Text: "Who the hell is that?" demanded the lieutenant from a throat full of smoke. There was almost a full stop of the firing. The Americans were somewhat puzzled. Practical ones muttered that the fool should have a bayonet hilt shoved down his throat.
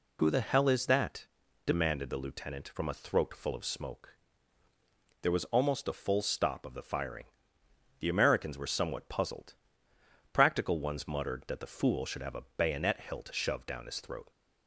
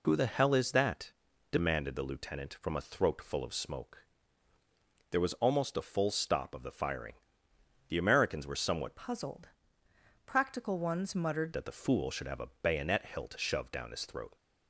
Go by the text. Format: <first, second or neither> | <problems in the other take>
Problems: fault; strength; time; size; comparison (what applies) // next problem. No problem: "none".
first | changes voice from "puzzled" to "muttered"; from 8.9 to 11.5 s; 2.6 s long